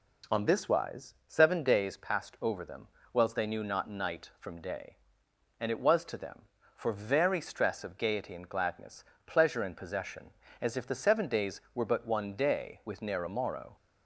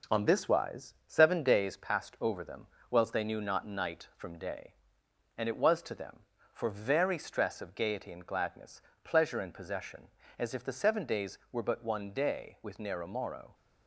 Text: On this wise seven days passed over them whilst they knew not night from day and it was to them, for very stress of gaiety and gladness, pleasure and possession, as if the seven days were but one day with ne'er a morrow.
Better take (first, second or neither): first